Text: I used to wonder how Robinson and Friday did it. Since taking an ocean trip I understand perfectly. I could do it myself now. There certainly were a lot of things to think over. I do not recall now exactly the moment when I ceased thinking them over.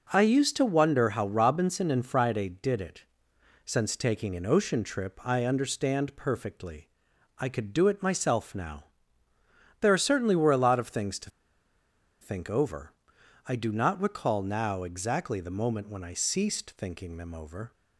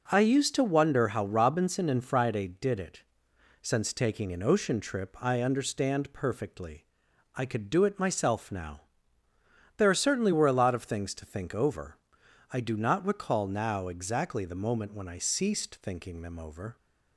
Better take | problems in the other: second | pauses between "to" and "think"; noticeable; at 11.2 s; 0.91 s long

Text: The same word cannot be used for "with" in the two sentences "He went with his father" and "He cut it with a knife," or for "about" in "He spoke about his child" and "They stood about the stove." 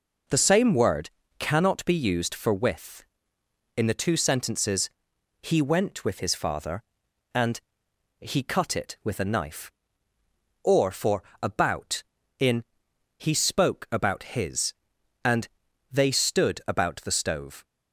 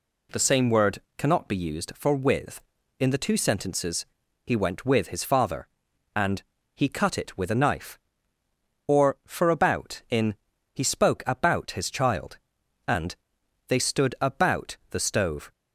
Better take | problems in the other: second | pauses between "word" and "cannot"; slight; at 1.0 s; 0.30 s long; slight in the second // pauses between "sentences" and "He"; noticeable; at 4.8 s; 0.52 s long; also in the second // pauses between "and" and "He"; noticeable; at 7.6 s; 0.58 s long; slight in the second // pauses between "for" and "about"; slight; at 11.2 s; 0.18 s long // pauses between "in" and "He"; noticeable; at 12.6 s; 0.54 s long; slight in the second // skips "child"; at 14.9 s // pauses between "and" and "They"; at 15.4 s; 0.44 s long; noticeable in the second

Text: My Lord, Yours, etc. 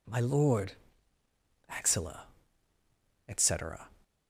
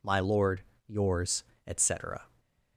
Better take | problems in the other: second | says "Axilla" for "Yours"; at 1.6 s

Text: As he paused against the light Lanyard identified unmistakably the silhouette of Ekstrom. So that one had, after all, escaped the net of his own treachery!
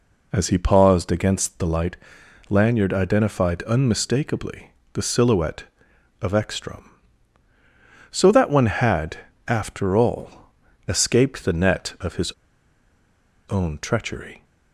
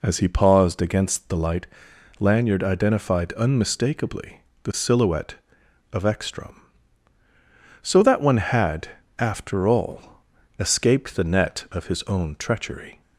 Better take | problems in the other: second | pauses between "light" and "Lanyard"; noticeable; at 1.9 s; 0.52 s long; noticeable in the second // pauses between "unmistakably" and "the"; slight; at 4.6 s; 0.24 s long; slight in the second // pauses between "his" and "own"; at 12.3 s; 1.1 s long

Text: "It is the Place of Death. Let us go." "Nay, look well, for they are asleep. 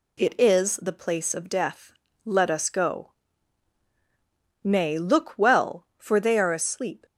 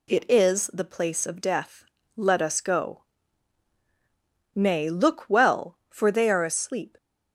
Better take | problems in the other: neither | none

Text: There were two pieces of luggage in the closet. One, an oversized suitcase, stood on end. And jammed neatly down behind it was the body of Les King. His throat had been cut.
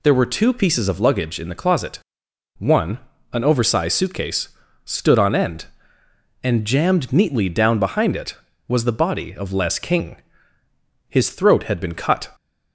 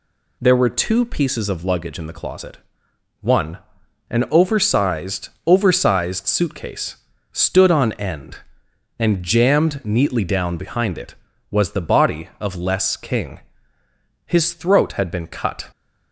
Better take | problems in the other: first | says "oversized" twice; at 5.4 s

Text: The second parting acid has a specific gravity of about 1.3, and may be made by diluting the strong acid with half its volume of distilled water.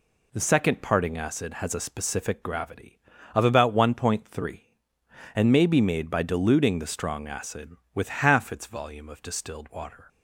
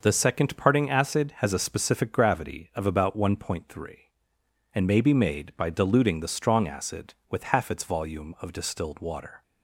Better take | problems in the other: neither | none

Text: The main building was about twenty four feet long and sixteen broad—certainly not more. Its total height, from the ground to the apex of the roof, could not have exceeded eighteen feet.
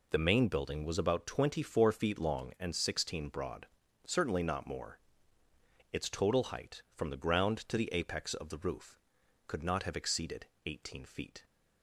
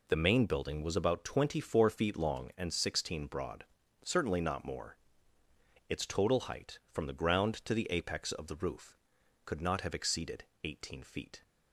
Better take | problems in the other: neither | pauses between "exceeded" and "eighteen"; slight; the same in both

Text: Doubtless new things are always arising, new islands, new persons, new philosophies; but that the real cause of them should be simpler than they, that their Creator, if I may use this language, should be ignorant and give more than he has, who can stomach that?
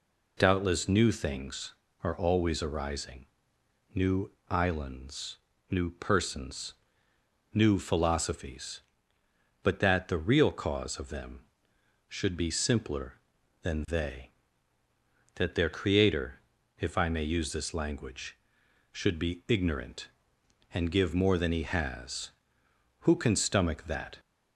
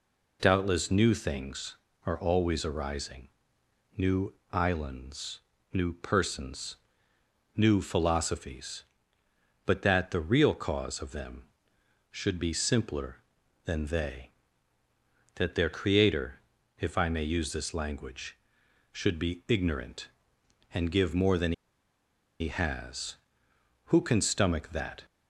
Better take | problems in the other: first | pauses between "new" and "islands"; slight; at 4.3 s; 0.18 s long; slight in the first // pauses between "than" and "he"; noticeable; at 21.5 s; 0.87 s long

